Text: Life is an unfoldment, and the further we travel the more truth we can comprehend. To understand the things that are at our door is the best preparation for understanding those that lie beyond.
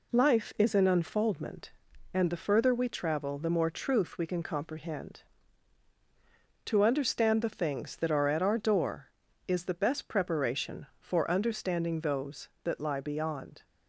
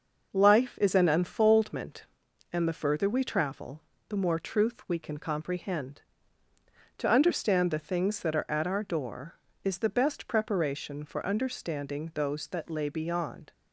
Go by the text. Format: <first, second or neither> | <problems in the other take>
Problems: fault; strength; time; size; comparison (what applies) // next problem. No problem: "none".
first | pauses between "travel" and "the"; slight; at 3.7 s; 0.30 s long // says "lay" for "lie"; at 12.7 s